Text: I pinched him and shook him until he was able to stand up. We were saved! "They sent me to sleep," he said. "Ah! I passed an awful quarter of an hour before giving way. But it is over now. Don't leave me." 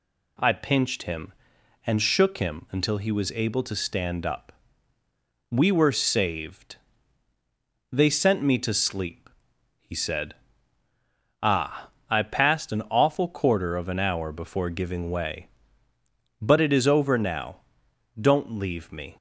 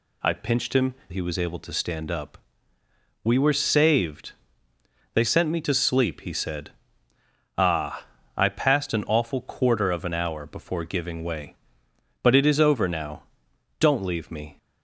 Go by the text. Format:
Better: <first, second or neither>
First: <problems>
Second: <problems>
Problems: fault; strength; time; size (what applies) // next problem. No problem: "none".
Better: first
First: none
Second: skips "and shook him until"; at 1.0 s